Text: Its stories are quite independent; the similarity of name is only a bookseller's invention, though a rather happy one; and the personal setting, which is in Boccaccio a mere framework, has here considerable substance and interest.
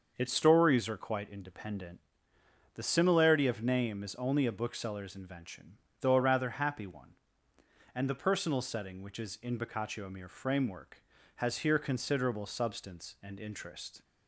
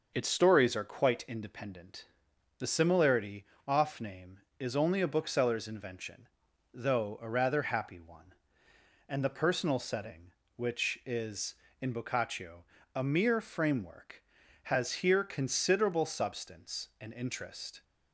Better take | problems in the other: first | starts louder than the rest; until 1.1 s; 6 dB; also in the first // says "off" for "of"; at 3.6 s // pauses between "Boccaccio" and "a"; slight; at 12.6 s; 0.30 s long

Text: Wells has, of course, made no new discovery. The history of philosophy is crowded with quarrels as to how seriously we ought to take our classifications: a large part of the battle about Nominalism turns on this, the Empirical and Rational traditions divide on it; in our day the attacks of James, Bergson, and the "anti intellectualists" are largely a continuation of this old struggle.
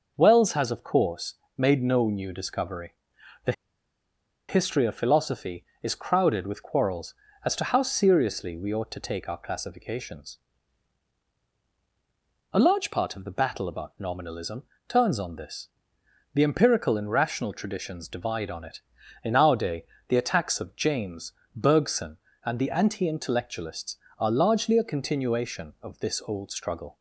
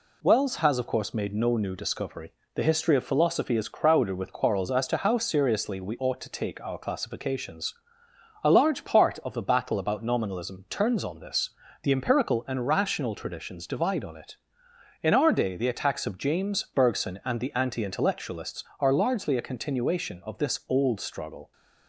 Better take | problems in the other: second | pauses between "The" and "history"; noticeable; at 3.5 s; 0.96 s long // pauses between "Nominalism" and "turns"; slight; at 14.6 s; 0.24 s long // pauses between "day" and "the"; slight; at 19.8 s; 0.22 s long

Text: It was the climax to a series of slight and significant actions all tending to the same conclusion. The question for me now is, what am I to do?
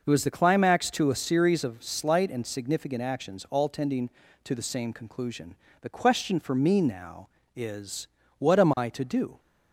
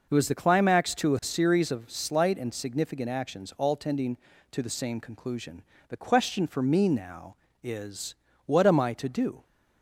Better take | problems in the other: neither | none

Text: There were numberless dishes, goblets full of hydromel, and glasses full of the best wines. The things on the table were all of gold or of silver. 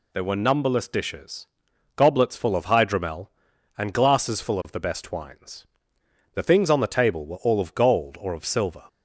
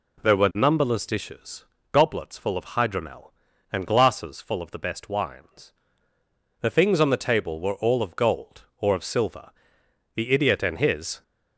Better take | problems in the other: first | goes on to say "The idiot and his"; noticeable; from 10.1 s on; 1.0 s long

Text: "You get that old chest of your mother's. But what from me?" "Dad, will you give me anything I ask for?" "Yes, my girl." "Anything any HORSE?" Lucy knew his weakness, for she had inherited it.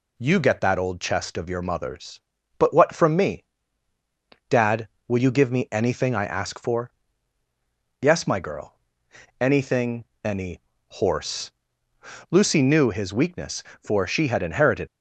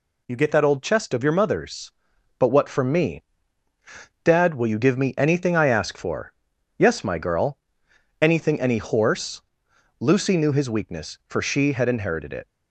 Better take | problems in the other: second | pauses between "Anything" and "any"; slight; at 10.0 s; 0.20 s long // pauses between "any" and "HORSE"; slight; at 10.5 s; 0.30 s long // stops before "it"; at 14.8 s

